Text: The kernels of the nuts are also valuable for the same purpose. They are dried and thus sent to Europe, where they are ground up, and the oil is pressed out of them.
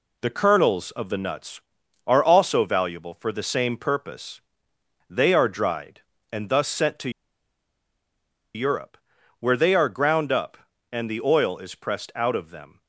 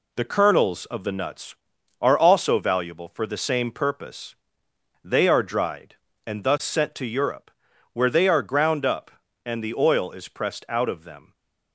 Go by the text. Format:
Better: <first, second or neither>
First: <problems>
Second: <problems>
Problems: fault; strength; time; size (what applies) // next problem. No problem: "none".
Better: second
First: pauses between "to" and "Europe"; strong; at 7.0 s; 1.4 s long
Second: none